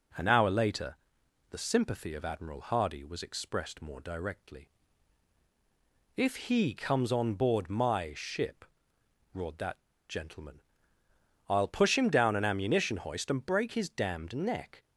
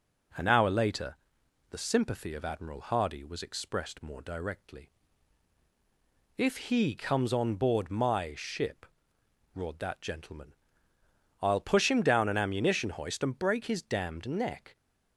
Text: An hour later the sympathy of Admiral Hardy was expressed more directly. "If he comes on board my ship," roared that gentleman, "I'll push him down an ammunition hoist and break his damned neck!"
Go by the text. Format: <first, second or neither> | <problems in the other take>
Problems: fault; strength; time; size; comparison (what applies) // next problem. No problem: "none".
second | pauses between "later" and "the"; noticeable; at 0.9 s; 0.56 s long; noticeable in the second // pauses between "that" and "gentleman"; slight; at 9.7 s; 0.29 s long